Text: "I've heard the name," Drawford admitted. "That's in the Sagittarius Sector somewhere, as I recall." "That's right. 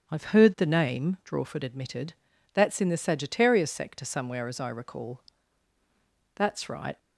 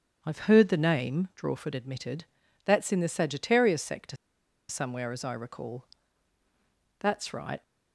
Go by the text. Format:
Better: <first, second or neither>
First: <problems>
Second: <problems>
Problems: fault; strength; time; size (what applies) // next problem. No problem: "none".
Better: first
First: starts louder than the rest; strong; until 1.1 s; 7.5 dB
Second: starts louder than the rest; strong; until 1.2 s; 7.5 dB // pauses between "Sector" and "somewhere"; noticeable; at 4.1 s; 0.53 s long